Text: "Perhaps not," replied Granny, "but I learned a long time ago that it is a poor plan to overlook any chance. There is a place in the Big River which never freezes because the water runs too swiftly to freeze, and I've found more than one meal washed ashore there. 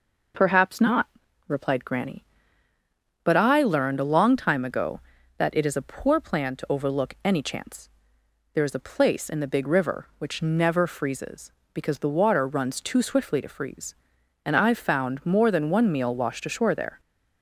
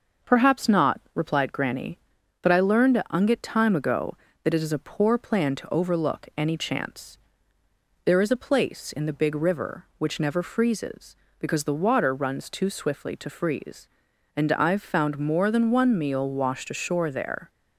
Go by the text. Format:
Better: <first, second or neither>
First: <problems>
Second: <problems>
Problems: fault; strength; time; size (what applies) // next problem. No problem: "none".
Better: first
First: none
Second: starts louder than the rest; until 1.4 s; 6.5 dB // says "unget" for "long"; at 3.0 s